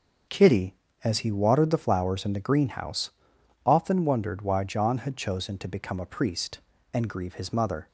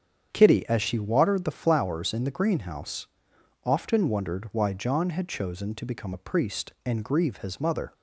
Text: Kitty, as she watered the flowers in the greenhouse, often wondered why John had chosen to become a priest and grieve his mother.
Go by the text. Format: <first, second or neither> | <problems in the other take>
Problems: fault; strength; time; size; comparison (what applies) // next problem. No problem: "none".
second | starts louder than the rest; until 1.5 s; 7 dB; strong in the second // says "he" for "she"; at 1.1 s